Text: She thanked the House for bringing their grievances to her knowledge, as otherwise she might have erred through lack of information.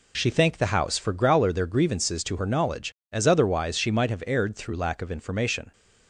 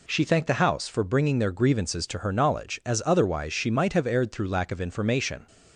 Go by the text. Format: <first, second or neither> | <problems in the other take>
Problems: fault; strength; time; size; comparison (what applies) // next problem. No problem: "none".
second | says "growler" for "bringing"; at 1.1 s